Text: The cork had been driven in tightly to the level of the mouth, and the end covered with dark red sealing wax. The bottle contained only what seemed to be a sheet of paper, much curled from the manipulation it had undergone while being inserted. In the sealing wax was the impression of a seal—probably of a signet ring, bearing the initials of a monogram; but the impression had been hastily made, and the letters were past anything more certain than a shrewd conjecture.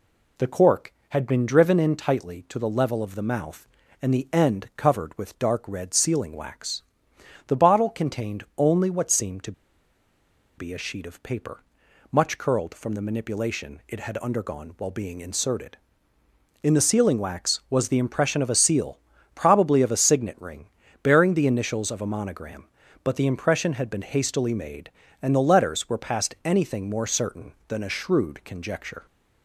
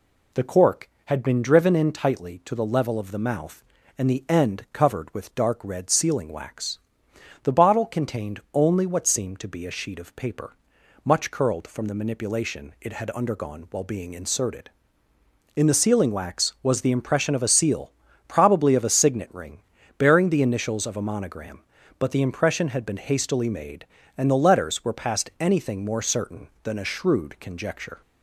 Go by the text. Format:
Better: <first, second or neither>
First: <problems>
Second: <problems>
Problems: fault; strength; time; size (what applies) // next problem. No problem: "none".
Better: second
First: pauses between "to" and "be"; at 9.5 s; 1.0 s long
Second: none